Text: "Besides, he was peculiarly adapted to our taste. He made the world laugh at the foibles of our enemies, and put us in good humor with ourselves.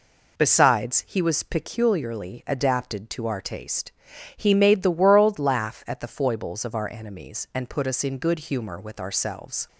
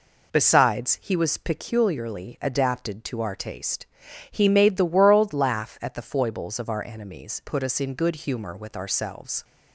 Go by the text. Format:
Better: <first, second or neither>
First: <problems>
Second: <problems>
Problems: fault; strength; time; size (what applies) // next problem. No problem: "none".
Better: first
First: none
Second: skips "and"; at 7.4 s